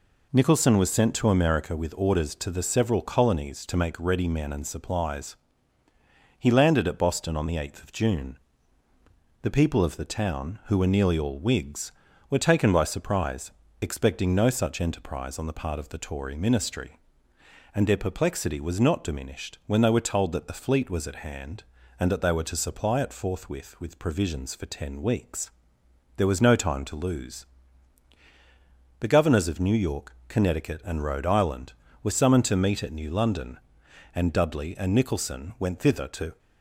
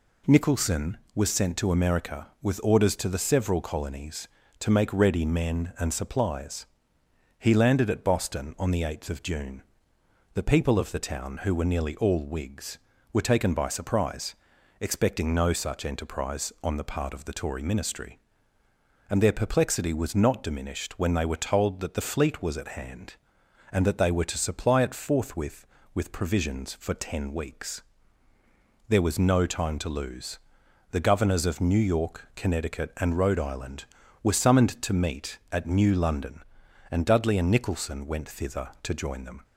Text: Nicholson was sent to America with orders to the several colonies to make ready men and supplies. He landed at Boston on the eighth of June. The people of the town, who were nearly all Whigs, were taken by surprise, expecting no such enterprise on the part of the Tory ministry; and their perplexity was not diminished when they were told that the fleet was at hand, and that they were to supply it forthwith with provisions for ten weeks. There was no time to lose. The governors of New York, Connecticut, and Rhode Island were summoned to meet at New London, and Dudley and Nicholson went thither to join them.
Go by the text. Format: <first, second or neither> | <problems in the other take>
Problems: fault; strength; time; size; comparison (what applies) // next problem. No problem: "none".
second | stops before "join them"; at 36.3 s